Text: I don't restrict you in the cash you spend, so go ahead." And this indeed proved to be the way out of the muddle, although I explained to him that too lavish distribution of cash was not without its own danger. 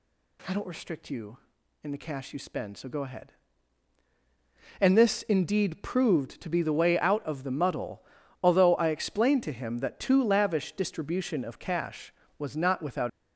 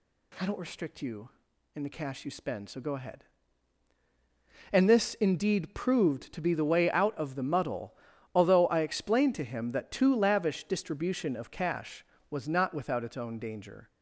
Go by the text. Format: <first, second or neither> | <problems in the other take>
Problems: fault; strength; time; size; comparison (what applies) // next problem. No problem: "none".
second | stops before "its own danger"; at 13.0 s